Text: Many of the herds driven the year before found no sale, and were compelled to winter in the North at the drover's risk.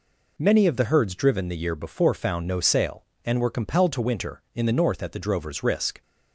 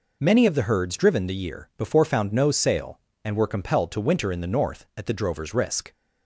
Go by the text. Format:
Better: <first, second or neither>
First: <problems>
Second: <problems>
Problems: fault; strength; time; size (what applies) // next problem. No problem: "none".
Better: neither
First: none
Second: none